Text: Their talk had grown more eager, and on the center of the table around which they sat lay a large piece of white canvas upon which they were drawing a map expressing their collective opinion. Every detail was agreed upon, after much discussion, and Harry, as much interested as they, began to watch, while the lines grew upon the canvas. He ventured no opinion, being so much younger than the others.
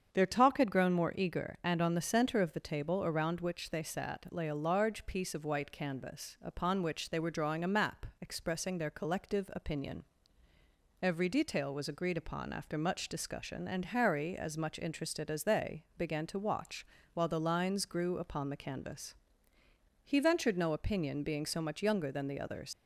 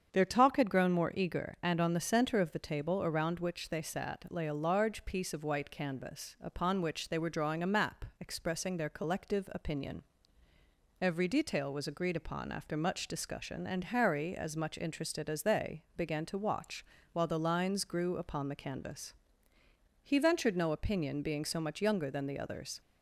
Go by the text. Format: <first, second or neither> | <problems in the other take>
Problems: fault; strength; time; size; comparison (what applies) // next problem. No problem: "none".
second | starts louder than the rest; strong; until 1.1 s; 7.5 dB; strong in the second // leaves "others" unfinished; at 22.7 s; 80 ms